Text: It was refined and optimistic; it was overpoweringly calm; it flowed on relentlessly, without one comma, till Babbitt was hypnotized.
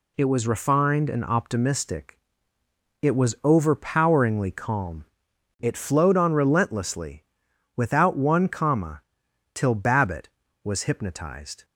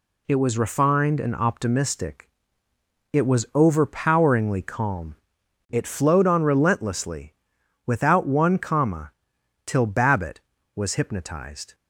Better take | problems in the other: neither | none

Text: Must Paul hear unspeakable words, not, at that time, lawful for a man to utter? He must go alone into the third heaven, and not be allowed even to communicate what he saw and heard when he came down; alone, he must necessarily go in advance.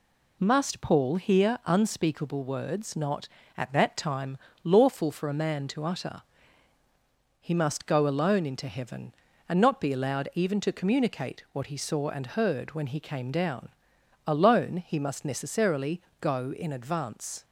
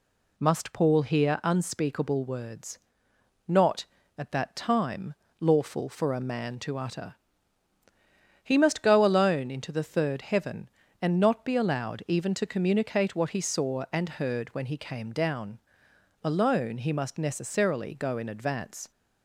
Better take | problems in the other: second | skips "the third"; at 8.6 s // pauses between "necessarily" and "go"; slight; at 16.0 s; 0.20 s long

